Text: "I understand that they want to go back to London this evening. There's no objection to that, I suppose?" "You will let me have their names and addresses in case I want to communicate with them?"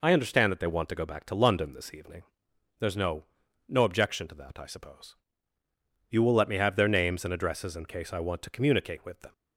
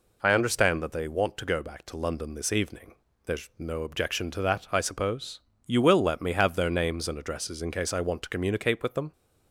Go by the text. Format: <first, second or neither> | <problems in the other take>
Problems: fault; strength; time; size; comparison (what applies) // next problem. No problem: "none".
second | says "no" twice; at 3.6 s